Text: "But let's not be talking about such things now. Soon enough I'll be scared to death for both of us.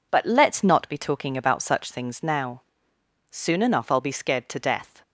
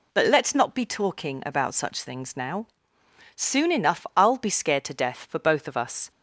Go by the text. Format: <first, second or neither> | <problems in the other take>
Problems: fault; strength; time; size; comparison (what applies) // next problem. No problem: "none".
second | stops before "for both of us"; at 5.0 s